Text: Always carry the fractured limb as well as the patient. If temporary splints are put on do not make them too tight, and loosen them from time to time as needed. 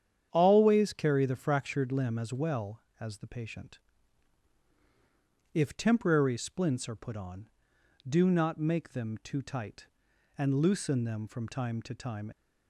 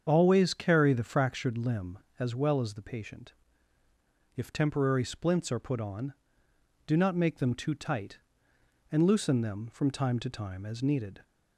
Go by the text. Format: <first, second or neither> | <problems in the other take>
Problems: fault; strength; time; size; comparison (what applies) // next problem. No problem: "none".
second | starts louder than the rest; strong; until 1.3 s; 9 dB; strong in the second // stops before "as needed"; at 12.3 s